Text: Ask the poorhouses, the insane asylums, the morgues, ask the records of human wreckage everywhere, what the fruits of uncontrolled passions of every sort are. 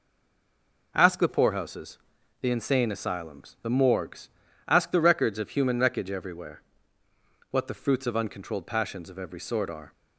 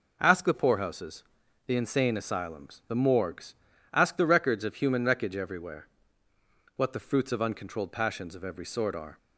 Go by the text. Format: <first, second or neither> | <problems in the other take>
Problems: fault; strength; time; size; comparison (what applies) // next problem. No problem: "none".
second | stays silent before the first word; slight; until 0.9 s; 0.9 s long